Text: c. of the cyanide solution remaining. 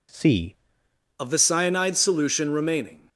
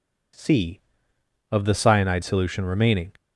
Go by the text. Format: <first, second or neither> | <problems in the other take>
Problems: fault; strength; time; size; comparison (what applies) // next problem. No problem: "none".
second | changes voice at "of"; from 1.1 s on; 1.9 s long